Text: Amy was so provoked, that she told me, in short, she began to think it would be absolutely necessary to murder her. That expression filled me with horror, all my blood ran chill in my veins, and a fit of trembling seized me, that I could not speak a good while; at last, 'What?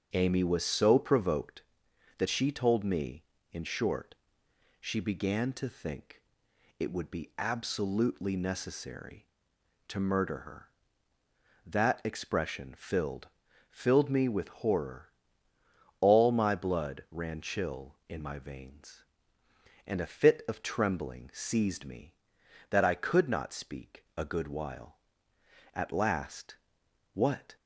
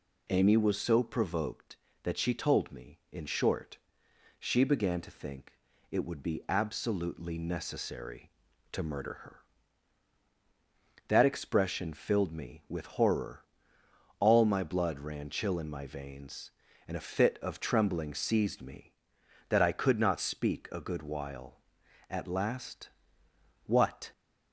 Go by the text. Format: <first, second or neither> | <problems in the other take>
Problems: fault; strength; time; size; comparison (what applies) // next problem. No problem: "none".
second | starts louder than the rest; until 1.1 s; 6.5 dB // pauses between "think" and "it"; noticeable; at 6.2 s; 0.58 s long; also in the second // says "filled" twice; at 13.6 s